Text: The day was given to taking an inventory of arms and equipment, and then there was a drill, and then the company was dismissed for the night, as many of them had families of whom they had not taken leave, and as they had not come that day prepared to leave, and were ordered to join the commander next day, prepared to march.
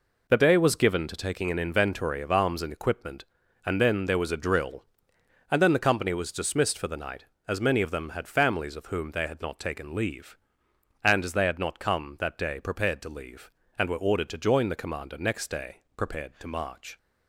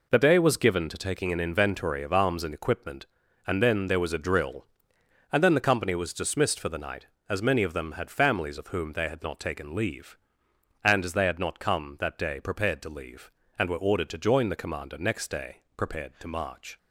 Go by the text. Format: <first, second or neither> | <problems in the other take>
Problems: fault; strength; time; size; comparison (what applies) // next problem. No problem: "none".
neither | none